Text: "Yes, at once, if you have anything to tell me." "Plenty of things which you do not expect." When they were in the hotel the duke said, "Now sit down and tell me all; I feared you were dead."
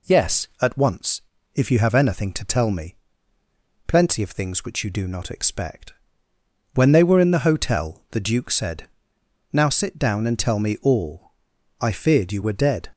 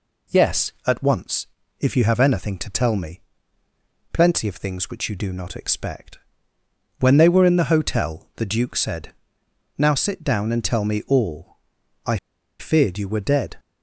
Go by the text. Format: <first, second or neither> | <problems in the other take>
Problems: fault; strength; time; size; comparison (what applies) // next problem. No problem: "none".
first | pauses between "I" and "feared"; at 12.1 s; 0.40 s long